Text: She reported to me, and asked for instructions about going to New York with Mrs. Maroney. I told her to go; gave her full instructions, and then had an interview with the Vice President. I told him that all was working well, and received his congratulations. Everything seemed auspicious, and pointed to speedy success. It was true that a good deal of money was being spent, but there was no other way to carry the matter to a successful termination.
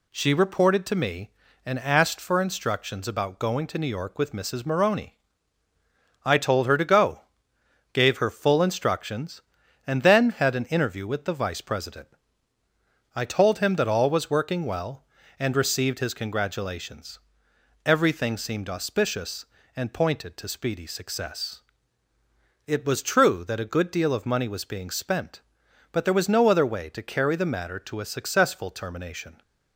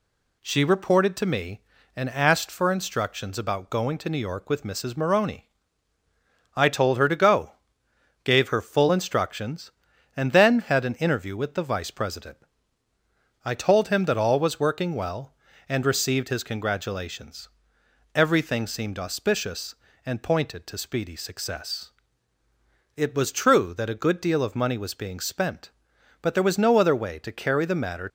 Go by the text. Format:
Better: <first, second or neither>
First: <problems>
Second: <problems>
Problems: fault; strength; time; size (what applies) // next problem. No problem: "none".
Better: first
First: none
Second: stops before "to a successful termination"; at 28.0 s